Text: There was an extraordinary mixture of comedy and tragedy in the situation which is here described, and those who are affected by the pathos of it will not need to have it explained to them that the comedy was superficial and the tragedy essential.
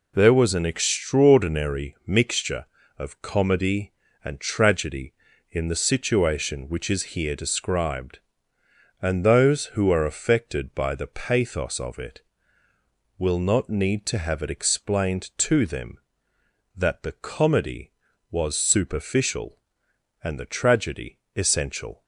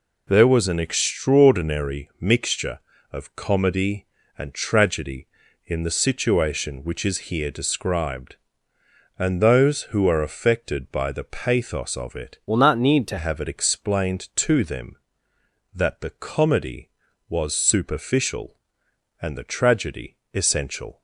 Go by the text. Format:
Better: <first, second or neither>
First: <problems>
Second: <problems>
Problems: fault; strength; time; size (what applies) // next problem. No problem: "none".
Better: first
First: pauses between "tragedy" and "essential"; slight; at 21.1 s; 0.18 s long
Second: changes voice from "will" to "to"; from 12.4 to 13.1 s; 0.7 s long // pauses between "tragedy" and "essential"; slight; at 20.1 s; 0.18 s long